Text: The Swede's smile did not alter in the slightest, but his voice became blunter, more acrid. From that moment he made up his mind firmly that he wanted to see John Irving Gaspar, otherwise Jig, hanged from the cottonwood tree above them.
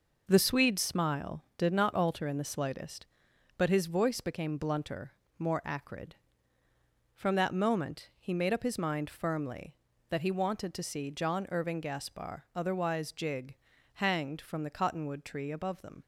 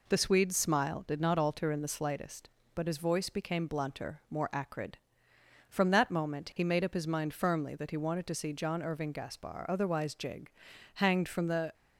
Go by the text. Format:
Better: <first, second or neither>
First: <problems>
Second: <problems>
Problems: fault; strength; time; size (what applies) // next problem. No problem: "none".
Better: first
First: none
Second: stops before "cottonwood tree above them"; at 11.7 s